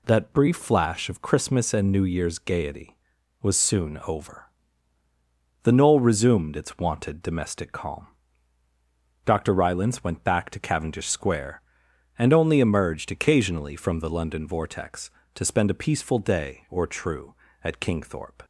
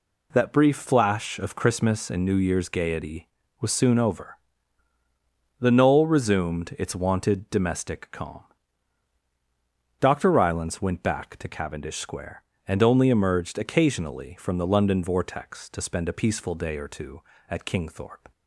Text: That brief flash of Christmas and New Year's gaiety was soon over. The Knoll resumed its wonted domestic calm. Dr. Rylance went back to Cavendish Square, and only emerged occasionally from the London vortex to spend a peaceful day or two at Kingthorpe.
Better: second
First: says "true" for "two"; at 16.8 s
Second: none

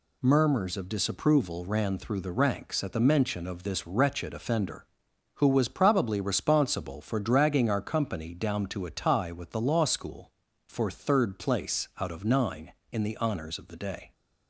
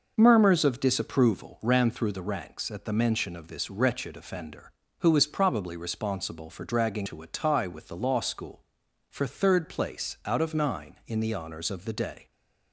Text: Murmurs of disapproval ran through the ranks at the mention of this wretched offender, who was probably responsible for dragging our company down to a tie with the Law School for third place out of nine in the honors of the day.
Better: first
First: none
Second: skips "our company down"; at 7.0 s

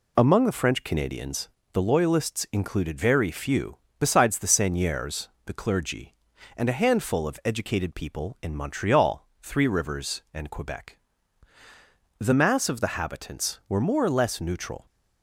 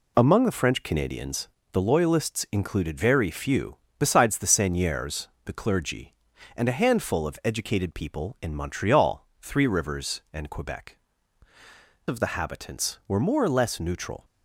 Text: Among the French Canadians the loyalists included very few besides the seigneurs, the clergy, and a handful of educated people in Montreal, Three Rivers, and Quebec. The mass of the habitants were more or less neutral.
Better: first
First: pauses between "Canadians" and "the"; slight; at 1.4 s; 0.24 s long // pauses between "few" and "besides"; slight; at 3.7 s; 0.22 s long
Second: pauses between "Canadians" and "the"; slight; at 1.4 s; 0.24 s long // pauses between "few" and "besides"; slight; at 3.7 s; 0.22 s long // skips "The mass"; at 11.5 s

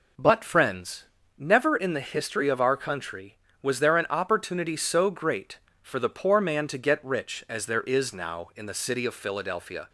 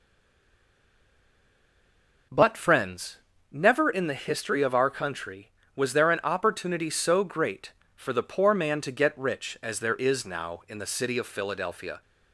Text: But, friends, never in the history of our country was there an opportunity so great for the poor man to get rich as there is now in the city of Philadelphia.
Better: first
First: none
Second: stays silent before the first word; until 2.3 s; 2.3 s long

